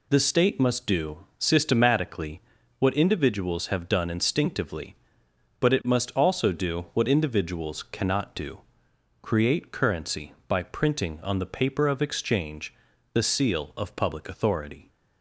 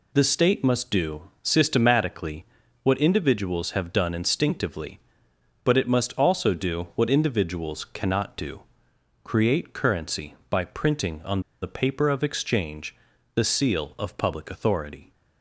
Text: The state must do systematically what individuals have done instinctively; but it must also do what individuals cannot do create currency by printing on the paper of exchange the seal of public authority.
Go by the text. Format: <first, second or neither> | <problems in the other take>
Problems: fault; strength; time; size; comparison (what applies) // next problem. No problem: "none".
first | pauses between "systematically" and "what"; at 2.4 s; 0.38 s long; also in the first // pauses between "do" and "create"; noticeable; at 8.6 s; 0.62 s long; noticeable in the first // pauses between "on" and "the"; slight; at 11.4 s; 0.21 s long // pauses between "exchange" and "the"; at 12.9 s; 0.38 s long; also in the first